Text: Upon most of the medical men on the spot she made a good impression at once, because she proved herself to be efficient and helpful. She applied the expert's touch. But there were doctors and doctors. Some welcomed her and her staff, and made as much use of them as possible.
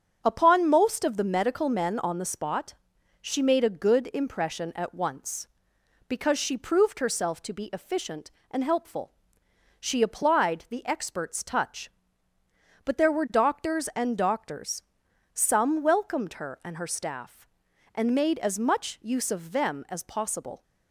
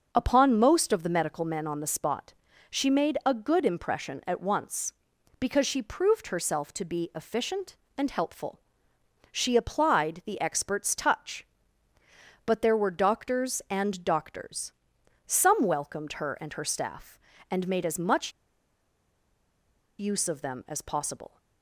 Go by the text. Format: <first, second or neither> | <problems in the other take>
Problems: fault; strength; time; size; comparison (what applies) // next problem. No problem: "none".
first | starts louder than the rest; noticeable; until 1.1 s; 6 dB; strong in the first // pauses between "spot" and "she"; at 2.3 s; 0.38 s long; noticeable in the first // pauses between "much" and "use"; strong; at 18.3 s; 1.6 s long